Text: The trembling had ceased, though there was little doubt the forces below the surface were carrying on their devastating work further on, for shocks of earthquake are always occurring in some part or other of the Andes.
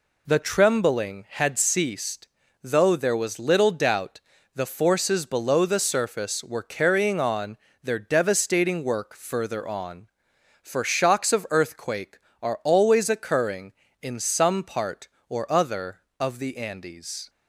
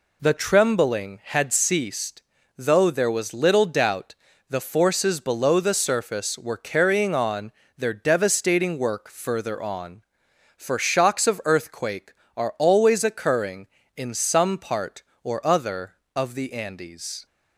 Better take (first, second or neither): neither